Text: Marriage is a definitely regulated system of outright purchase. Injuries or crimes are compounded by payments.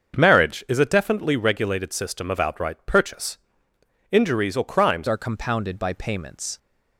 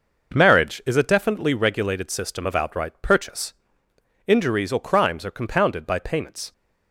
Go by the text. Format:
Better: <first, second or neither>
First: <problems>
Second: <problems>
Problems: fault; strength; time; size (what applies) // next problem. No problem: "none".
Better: second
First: starts louder than the rest; until 1.2 s; 6.5 dB // changes voice at "are"; from 5.0 s on; 1.5 s long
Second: none